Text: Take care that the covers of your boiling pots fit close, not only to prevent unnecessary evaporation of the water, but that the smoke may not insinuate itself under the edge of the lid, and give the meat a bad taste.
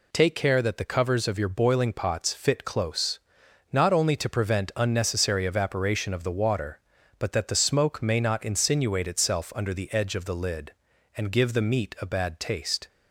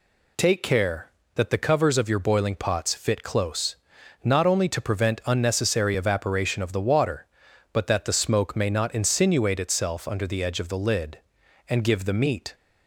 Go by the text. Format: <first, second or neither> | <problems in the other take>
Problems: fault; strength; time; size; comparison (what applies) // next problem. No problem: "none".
first | stops before "a bad taste"; at 12.5 s